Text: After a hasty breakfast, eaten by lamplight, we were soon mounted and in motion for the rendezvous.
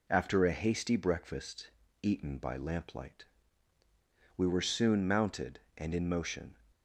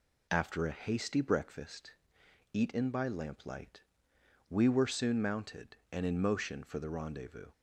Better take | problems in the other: second | stops before "for the rendezvous"; at 6.7 s

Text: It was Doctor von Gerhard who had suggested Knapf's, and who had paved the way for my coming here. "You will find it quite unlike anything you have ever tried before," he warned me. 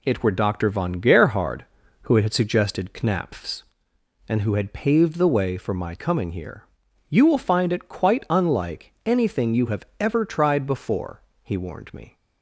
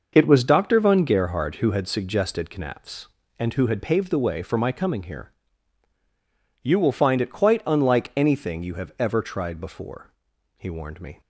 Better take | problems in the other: second | says "were" for "was"; at 0.2 s

